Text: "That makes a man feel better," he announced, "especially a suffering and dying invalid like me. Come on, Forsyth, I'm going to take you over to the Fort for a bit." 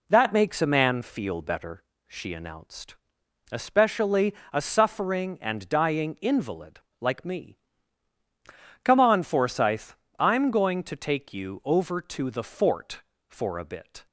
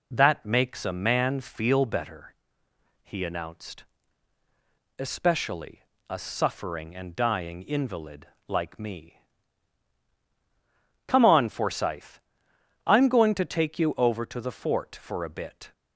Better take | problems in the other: second | says "she" for "he"; at 2.0 s // pauses between "especially" and "a"; slight; at 4.3 s; 0.16 s long; slight in the second // pauses between "invalid" and "like"; slight; at 6.7 s; 0.20 s long; slight in the second

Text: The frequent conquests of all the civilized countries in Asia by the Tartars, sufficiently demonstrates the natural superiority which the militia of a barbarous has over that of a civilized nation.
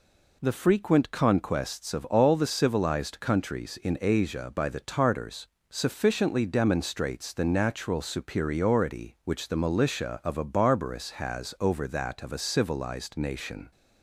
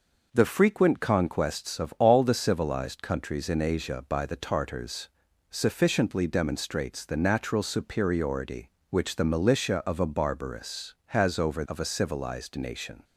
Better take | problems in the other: first | skips "that"; at 11.6 s

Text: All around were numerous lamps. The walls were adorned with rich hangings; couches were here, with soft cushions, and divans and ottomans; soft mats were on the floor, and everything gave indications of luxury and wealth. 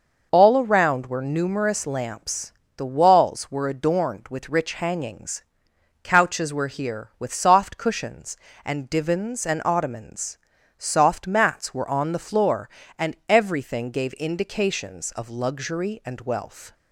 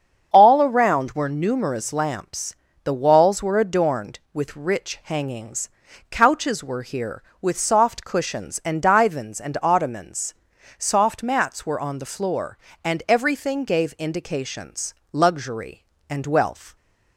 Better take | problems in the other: first | starts louder than the rest; strong; until 1.3 s; 7.5 dB // skips "of"; at 15.0 s

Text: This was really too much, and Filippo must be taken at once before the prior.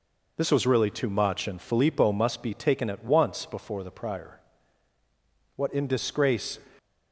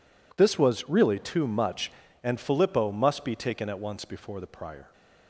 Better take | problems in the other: second | goes on to say "What in disgrace"; noticeable; from 5.5 s on; 1.0 s long

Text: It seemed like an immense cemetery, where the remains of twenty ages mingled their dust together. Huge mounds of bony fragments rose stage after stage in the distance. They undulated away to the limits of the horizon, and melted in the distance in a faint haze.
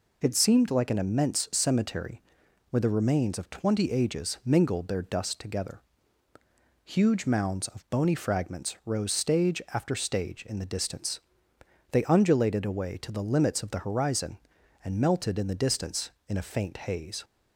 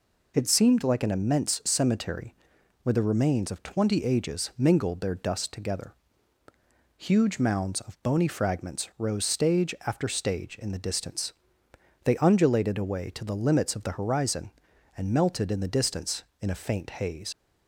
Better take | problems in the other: first | leaves "haze" unfinished; at 17.3 s; 40 ms

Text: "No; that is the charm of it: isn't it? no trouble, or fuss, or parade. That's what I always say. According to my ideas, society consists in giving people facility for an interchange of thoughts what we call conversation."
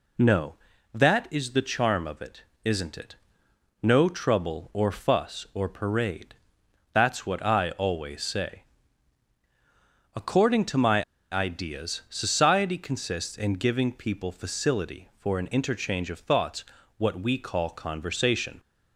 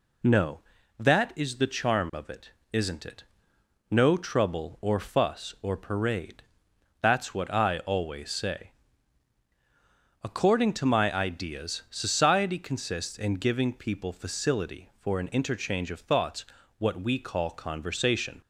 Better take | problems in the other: second | pauses between "my" and "ideas"; slight; at 11.0 s; 0.29 s long // pauses between "thoughts" and "what"; slight; at 16.6 s; 0.32 s long; slight in the second

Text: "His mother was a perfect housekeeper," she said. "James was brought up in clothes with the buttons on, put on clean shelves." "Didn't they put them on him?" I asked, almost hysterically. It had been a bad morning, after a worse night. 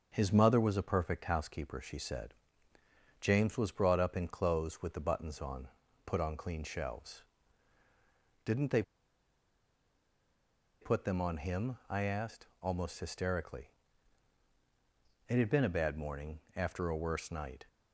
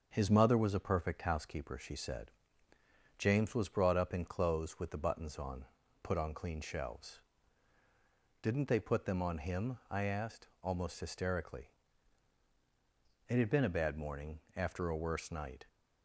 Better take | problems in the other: second | starts louder than the rest; until 1.1 s; 6 dB; also in the second // pauses between "they" and "put"; strong; at 8.8 s; 1.9 s long

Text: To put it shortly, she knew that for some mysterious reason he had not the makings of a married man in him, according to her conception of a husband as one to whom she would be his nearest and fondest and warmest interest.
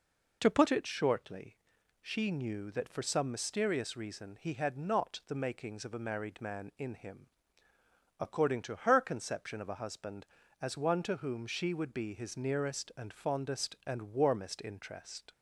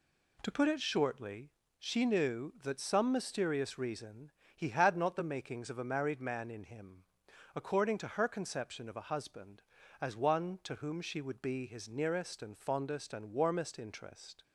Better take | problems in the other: first | skips "for"; at 2.7 s // pauses between "reason" and "he"; slight; at 4.3 s; 0.24 s long

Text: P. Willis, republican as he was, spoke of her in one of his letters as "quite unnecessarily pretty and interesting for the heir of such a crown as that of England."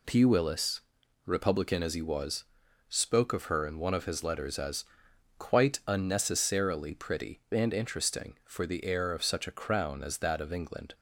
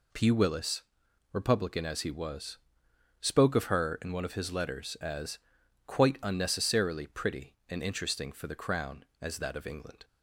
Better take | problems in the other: first | pauses between "as" and "quite"; noticeable; at 5.3 s; 0.48 s long; noticeable in the first // skips "heir of such a"; at 8.5 s

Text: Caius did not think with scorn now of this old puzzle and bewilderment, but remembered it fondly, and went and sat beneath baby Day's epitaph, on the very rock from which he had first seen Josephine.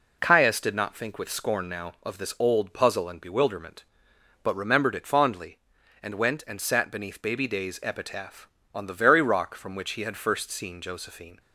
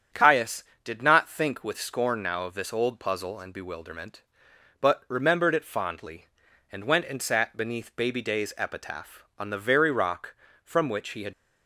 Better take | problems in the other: first | starts louder than the rest; strong; until 1.3 s; 8.5 dB // stops before "first seen Josephine"; at 11.3 s

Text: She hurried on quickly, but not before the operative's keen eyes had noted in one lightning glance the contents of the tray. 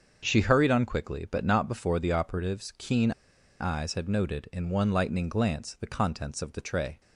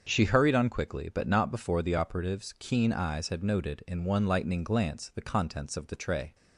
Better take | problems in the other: second | starts louder than the rest; until 1.2 s; 6.5 dB; also in the second // pauses between "keen" and "eyes"; noticeable; at 3.1 s; 0.48 s long

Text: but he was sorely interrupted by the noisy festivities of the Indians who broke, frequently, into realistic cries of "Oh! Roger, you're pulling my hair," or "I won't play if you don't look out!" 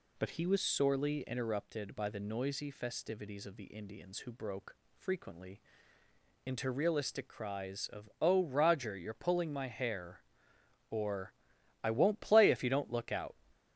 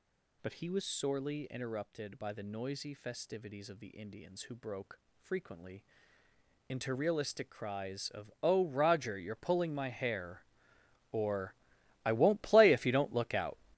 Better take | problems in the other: first | gets louder; strong; throughout; 11.5 dB // pauses between "or" and "I"; noticeable; at 11.5 s; 0.50 s long; noticeable in the first

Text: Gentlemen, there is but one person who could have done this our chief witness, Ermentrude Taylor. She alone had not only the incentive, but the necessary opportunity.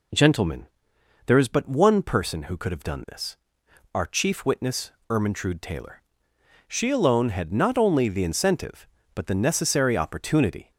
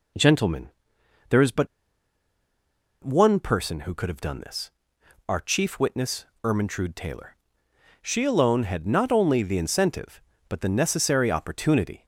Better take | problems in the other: first | pauses between "but" and "one"; strong; at 1.6 s; 1.3 s long // pauses between "this" and "our"; noticeable; at 4.7 s; 0.58 s long; noticeable in the first

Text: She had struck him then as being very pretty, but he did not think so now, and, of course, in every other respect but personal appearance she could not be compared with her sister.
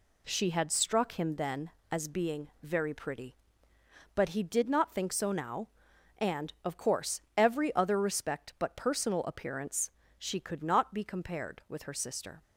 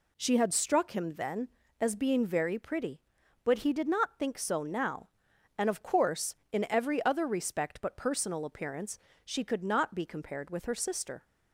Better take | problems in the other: second | pauses between "being" and "very"; slight; at 2.4 s; 0.16 s long // skips "in"; at 7.2 s // pauses between "appearance" and "she"; slight; at 9.9 s; 0.26 s long; slight in the second

